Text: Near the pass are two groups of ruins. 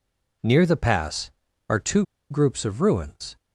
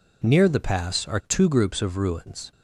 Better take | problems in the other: second | pauses between "two" and "groups"; slight; at 2.0 s; 0.25 s long

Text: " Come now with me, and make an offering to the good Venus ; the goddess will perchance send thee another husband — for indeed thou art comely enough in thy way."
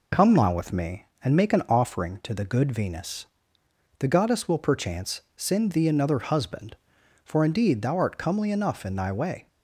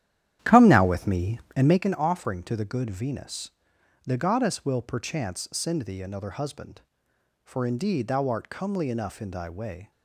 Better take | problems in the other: first | starts louder than the rest; strong; until 1.9 s; 11 dB

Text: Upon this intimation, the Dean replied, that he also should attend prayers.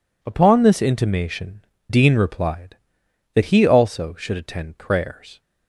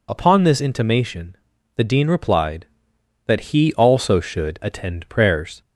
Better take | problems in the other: second | skips "the"; at 1.7 s

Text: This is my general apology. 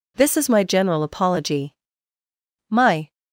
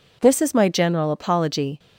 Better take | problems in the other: second | goes on to say "My"; slight; from 2.6 s on; 0.44 s long

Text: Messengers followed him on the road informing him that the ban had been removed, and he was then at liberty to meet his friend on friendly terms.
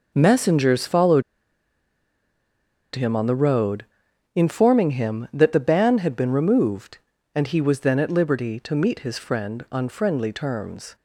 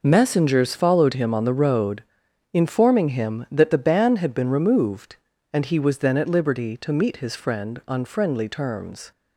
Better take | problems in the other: second | pauses between "followed" and "him"; strong; at 1.2 s; 1.7 s long // pauses between "road" and "informing"; noticeable; at 3.8 s; 0.50 s long; noticeable in the second

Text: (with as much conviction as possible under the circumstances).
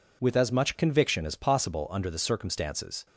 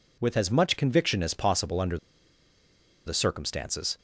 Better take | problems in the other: first | pauses between "under" and "the"; at 1.9 s; 1.0 s long

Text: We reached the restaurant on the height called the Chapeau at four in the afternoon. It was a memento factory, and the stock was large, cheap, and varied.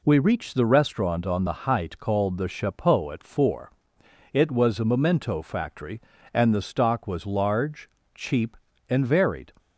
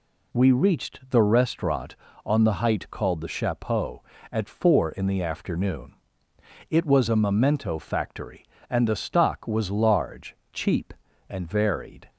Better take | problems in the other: second | skips "in the afternoon"; at 4.0 s

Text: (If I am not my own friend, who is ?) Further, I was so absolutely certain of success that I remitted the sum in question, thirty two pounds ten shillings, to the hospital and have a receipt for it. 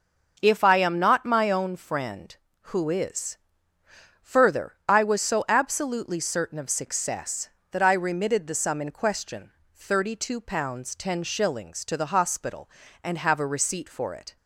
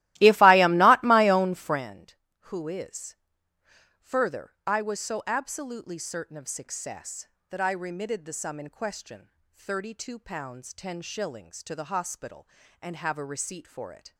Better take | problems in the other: first | starts louder than the rest; strong; until 1.8 s; 16 dB

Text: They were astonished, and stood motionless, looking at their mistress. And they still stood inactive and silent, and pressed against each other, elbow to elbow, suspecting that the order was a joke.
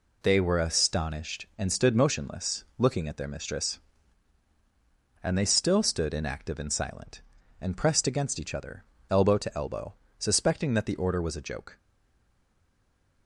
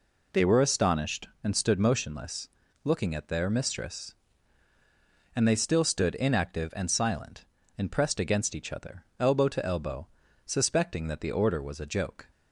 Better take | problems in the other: second | stays silent after the last word; noticeable; from 11.7 s on; 1.5 s long

